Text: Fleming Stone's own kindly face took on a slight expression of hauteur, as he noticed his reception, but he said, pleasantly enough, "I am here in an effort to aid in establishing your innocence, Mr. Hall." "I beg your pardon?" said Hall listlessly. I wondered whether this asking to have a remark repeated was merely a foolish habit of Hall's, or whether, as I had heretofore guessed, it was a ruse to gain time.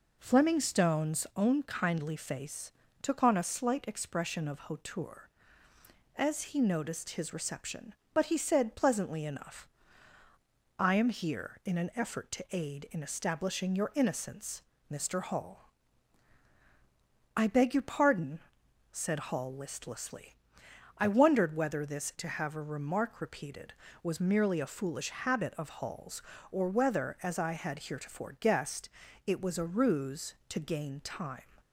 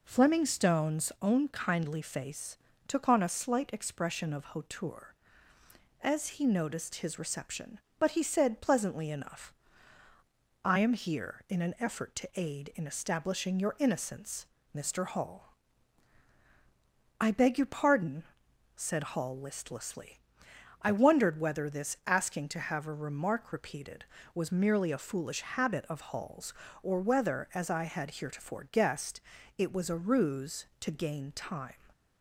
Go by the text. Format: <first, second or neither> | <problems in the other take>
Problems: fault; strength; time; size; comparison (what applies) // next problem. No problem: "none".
second | pauses between "face" and "took"; slight; at 2.7 s; 0.30 s long; slight in the second // skips "asking"; at 22.1 s